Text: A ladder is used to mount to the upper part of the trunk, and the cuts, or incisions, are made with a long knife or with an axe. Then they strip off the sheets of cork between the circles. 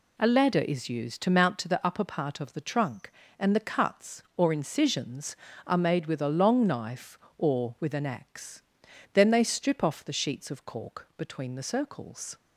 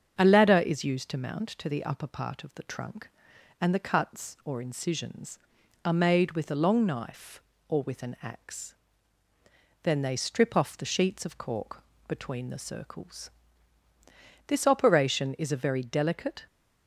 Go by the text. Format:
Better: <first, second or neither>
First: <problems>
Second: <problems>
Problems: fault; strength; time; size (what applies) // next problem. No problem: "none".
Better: first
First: none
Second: starts louder than the rest; strong; until 1.1 s; 7 dB // pauses between "cork" and "between"; slight; at 11.8 s; 0.24 s long // goes on to say "This operation is a very delicate"; strong; from 14.4 s on; 2.0 s long